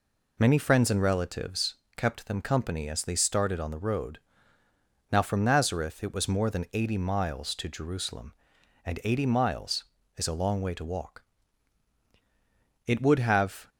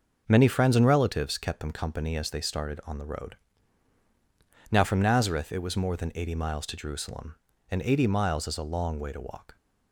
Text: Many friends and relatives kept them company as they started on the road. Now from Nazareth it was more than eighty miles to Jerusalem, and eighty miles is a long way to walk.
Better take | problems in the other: second | pauses between "relatives" and "kept"; slight; at 1.7 s; 0.20 s long // goes on to say "It would have"; noticeable; from 12.8 s on; 0.82 s long

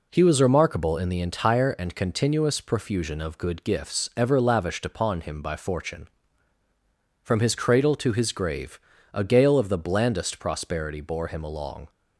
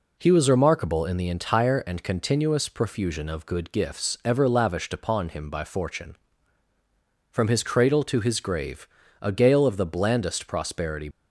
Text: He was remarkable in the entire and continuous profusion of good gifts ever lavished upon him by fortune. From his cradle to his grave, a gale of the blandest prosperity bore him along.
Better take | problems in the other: first | stops before "bore him along"; at 11.1 s

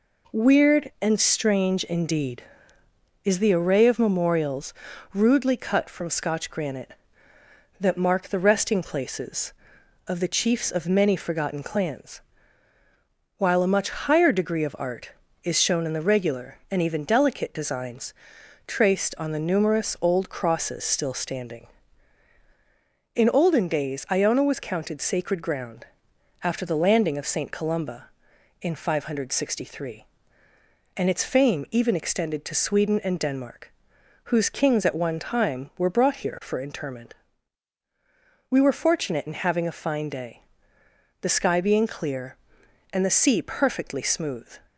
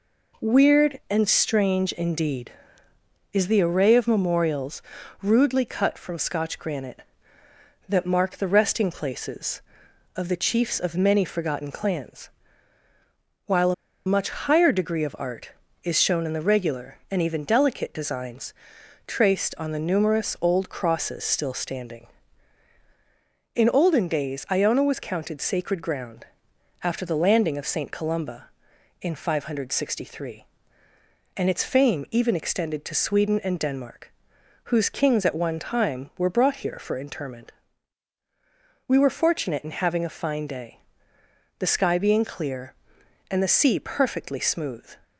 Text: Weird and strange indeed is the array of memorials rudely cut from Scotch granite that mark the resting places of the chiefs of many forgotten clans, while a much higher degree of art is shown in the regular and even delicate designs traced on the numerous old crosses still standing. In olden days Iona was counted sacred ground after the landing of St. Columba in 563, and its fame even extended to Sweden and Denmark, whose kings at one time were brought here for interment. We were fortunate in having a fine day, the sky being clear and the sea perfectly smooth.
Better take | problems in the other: first | pauses between "memorials" and "rudely"; at 4.8 s; 0.40 s long; also in the first // pauses between "a" and "much"; slight; at 13.7 s; 0.33 s long // pauses between "designs" and "traced"; noticeable; at 18.5 s; 0.54 s long; noticeable in the first // pauses between "ground" and "after"; noticeable; at 26.2 s; 0.56 s long; noticeable in the first

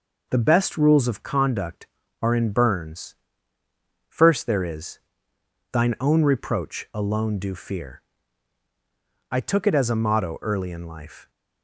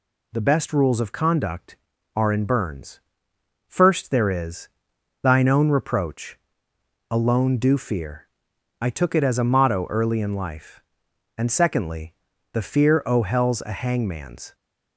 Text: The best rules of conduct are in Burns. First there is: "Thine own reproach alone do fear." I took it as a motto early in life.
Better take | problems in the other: first | pauses between "reproach" and "alone"; noticeable; at 6.3 s; 0.72 s long // goes on to say "And secondly The fear o hell's a hangman's"; strong; from 11.3 s on; 3.1 s long

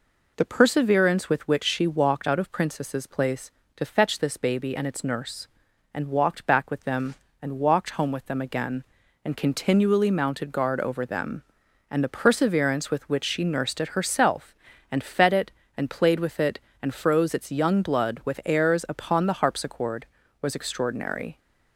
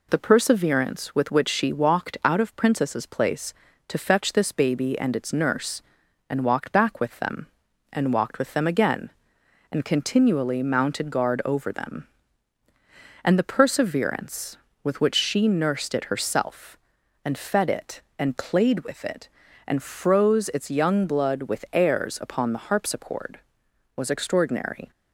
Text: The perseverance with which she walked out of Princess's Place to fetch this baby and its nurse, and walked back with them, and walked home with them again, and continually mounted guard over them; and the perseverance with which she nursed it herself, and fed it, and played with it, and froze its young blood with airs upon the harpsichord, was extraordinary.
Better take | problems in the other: first | skips "home"; at 8.3 s

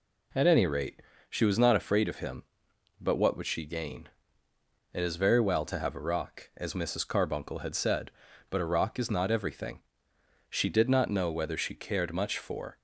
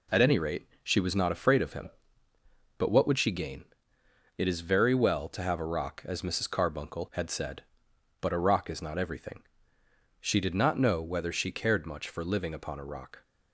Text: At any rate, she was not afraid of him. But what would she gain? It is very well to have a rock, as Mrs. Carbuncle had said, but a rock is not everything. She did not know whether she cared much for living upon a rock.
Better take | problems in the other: second | stops before "living upon a rock"; at 12.7 s

